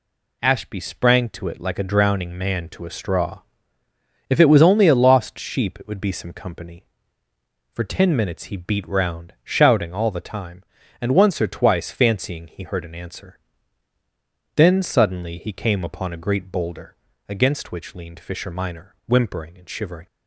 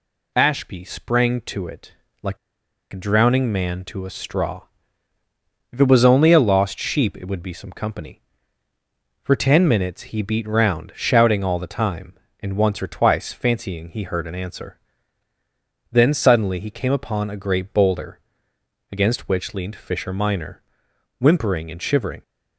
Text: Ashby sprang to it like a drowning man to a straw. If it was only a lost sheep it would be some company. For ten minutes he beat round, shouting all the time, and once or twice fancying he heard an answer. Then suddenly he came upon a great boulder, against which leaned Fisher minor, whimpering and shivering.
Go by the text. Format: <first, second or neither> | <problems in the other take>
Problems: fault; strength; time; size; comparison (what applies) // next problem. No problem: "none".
first | pauses between "it" and "like"; slight; at 1.9 s; 0.30 s long // pauses between "like" and "a"; noticeable; at 2.3 s; 0.54 s long